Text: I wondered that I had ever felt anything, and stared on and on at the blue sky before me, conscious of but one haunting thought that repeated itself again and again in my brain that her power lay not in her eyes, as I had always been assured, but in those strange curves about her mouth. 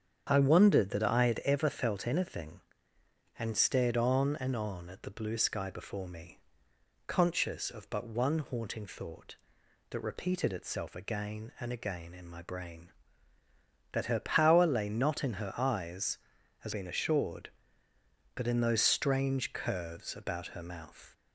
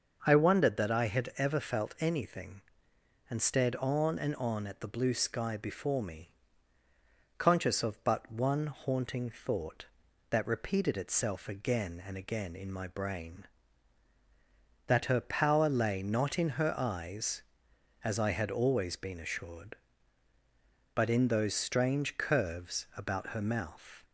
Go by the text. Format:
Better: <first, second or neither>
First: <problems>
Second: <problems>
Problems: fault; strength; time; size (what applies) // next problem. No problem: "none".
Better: second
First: starts louder than the rest; strong; until 1.3 s; 8 dB // skips "I had always"; at 16.7 s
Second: starts louder than the rest; until 1.2 s; 6.5 dB